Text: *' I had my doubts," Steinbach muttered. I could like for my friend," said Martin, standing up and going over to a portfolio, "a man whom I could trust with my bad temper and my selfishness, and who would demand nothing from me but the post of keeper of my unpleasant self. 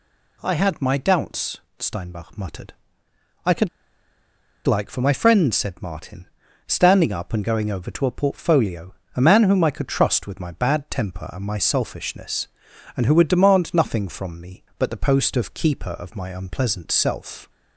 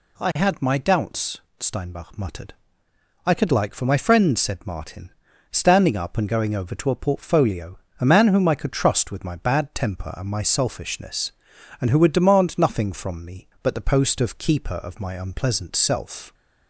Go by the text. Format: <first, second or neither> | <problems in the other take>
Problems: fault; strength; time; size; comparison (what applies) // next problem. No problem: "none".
second | pauses between "could" and "like"; at 3.6 s; 0.98 s long